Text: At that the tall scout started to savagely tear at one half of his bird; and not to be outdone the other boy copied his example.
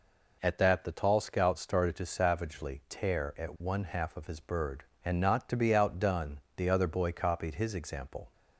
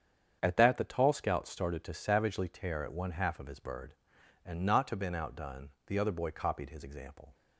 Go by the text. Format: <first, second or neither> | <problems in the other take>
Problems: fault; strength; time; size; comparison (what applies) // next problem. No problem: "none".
first | starts louder than the rest; strong; until 1.4 s; 8 dB // says "been" for "be"; at 4.9 s // pauses between "outdone" and "the"; slight; at 5.6 s; 0.18 s long; slight in the first